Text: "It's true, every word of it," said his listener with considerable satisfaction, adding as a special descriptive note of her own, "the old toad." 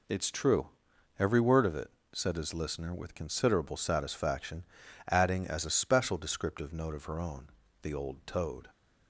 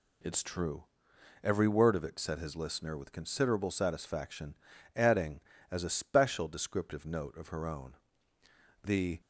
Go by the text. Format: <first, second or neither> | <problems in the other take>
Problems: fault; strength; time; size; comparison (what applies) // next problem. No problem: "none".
first | stops before "old toad"; at 9.2 s